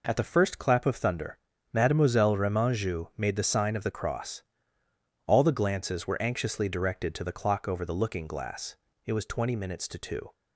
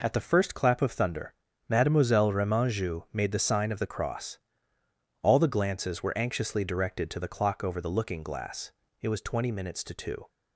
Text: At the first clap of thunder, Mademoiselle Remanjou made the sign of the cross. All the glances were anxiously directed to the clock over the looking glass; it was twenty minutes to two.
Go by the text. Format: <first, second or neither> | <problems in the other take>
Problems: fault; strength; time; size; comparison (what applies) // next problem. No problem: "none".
neither | none